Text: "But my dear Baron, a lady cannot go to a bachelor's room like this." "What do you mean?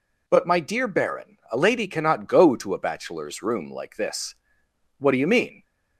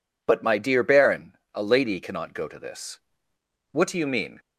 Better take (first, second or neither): first